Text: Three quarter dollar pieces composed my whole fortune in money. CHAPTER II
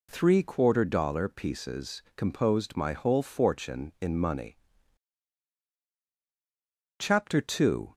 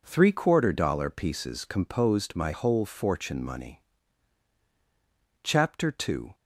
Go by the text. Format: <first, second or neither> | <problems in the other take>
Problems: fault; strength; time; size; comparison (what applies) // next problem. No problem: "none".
first | skips "in"; at 3.4 s